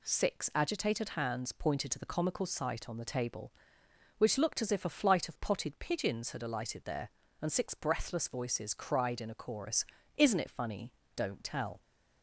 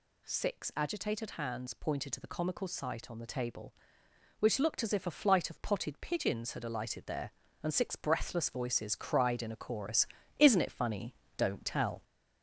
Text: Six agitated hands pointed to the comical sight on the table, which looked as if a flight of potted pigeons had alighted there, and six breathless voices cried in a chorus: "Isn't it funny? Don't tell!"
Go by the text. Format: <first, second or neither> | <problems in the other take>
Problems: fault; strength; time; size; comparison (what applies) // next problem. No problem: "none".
first | gets louder; noticeable; throughout; 4 dB